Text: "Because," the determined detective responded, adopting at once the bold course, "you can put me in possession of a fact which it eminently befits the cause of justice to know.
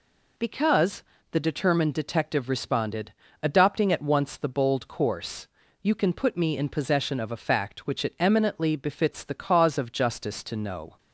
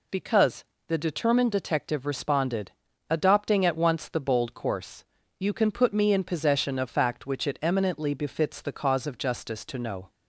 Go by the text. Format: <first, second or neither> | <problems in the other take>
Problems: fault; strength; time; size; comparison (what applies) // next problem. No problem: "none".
first | skips "a"; at 6.8 s